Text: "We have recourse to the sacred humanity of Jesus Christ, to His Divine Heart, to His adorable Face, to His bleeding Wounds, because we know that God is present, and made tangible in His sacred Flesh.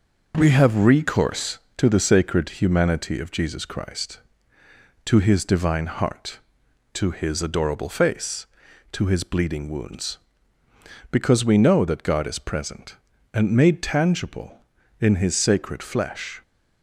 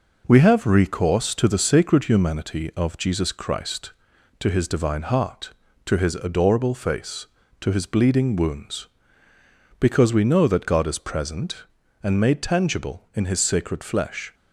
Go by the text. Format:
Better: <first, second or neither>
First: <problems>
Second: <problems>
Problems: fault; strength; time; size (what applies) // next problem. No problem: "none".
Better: neither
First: none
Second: none